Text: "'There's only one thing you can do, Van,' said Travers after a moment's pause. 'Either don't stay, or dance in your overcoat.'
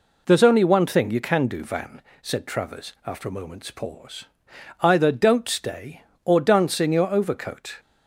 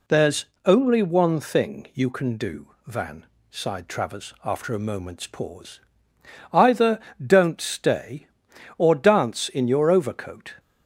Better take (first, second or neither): first